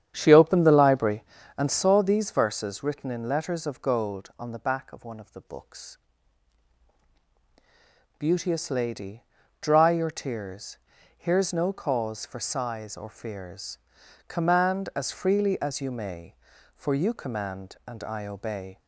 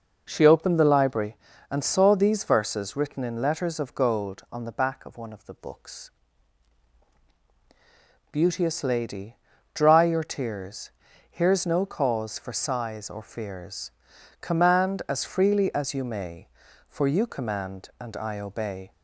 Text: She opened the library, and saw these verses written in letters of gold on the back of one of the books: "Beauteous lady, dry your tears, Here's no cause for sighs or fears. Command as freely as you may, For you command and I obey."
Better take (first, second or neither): second